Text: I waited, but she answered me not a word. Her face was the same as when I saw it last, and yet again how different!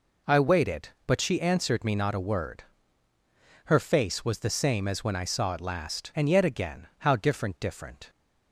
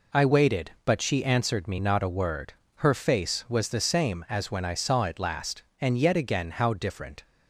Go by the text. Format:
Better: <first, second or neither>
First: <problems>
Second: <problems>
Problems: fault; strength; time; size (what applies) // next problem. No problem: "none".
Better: second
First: says "different" twice; at 7.5 s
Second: none